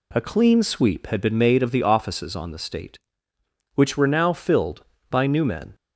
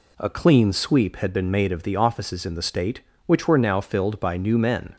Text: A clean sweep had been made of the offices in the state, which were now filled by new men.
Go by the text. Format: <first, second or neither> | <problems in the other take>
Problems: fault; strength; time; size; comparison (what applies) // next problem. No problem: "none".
second | says "on" for "in"; at 2.3 s